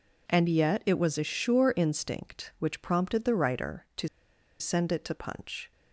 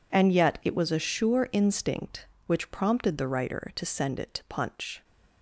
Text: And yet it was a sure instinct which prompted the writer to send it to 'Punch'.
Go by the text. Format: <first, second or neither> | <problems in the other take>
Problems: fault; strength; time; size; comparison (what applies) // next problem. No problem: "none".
second | pauses between "to" and "send"; noticeable; at 4.0 s; 0.52 s long